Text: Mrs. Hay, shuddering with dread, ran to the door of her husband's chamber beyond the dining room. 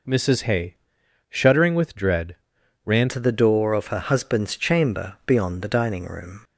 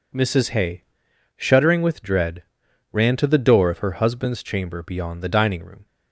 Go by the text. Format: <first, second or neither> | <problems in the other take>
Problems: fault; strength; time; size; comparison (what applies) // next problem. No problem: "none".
second | changes voice at "to"; from 3.0 s on; 3.4 s long